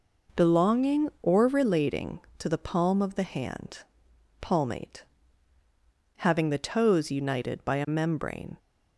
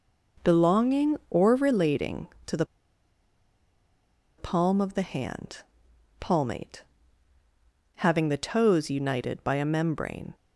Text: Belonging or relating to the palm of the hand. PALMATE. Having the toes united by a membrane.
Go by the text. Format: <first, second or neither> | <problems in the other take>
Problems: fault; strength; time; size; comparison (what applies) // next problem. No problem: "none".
first | pauses between "the" and "palm"; strong; at 2.6 s; 1.7 s long